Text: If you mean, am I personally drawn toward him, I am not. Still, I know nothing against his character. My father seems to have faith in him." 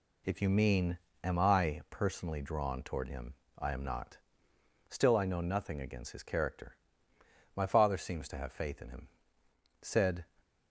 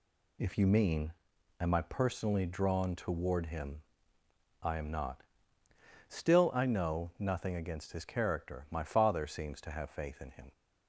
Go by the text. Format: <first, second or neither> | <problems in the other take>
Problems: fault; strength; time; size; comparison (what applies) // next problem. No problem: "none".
second | goes on to say "Said"; slight; from 9.8 s on; 0.44 s long